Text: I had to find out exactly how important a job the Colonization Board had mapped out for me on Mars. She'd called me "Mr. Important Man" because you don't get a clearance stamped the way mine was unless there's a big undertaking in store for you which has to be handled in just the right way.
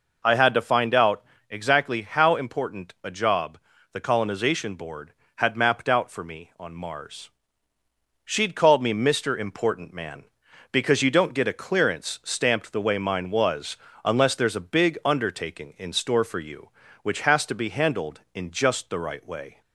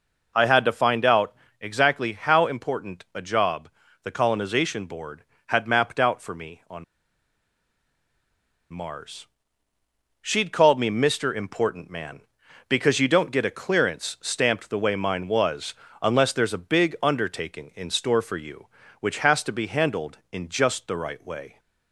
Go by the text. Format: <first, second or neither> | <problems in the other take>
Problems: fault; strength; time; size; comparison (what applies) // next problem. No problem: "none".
first | pauses between "out" and "exactly"; slight; at 1.3 s; 0.26 s long; slight in the first // pauses between "job" and "the"; slight; at 3.6 s; 0.34 s long; slight in the first // pauses between "on" and "Mars"; strong; at 6.8 s; 1.8 s long // pauses between "was" and "unless"; slight; at 15.7 s; 0.28 s long; slight in the first